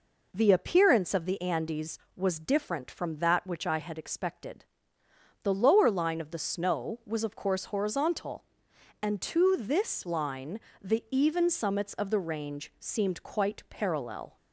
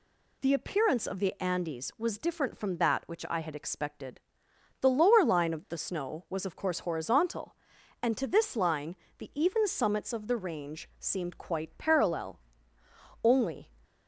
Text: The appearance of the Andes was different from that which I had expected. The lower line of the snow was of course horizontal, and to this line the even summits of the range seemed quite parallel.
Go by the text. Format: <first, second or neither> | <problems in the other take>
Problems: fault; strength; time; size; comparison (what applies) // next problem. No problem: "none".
first | pauses between "line" and "the"; slight; at 8.9 s; 0.24 s long; slight in the first // goes on to say "Only"; slight; from 13.2 s on; 0.48 s long